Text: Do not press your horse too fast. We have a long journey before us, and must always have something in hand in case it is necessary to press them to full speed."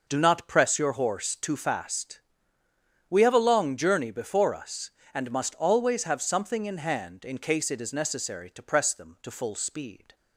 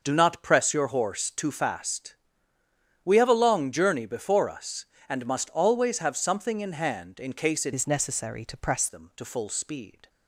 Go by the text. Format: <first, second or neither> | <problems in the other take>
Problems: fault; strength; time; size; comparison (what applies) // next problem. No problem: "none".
first | starts louder than the rest; noticeable; until 1.0 s; 6 dB // changes voice from "is" to "press"; from 7.7 to 8.8 s; 1.1 s long